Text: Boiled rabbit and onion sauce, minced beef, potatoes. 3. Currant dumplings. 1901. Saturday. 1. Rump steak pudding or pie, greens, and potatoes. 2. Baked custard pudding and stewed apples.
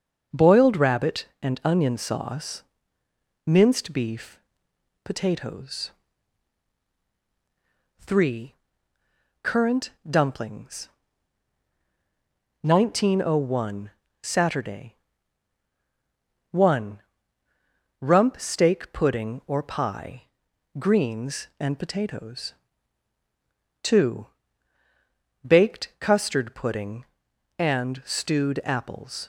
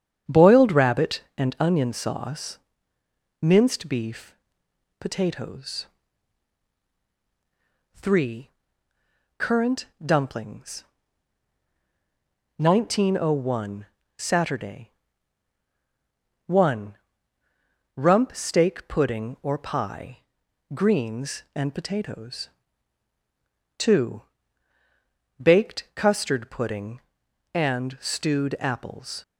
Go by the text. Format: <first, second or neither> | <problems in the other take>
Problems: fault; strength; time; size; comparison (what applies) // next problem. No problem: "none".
first | starts louder than the rest; strong; until 1.7 s; 8.5 dB // pauses between "Currant" and "dumplings"; slight; at 9.8 s; 0.18 s long; slight in the first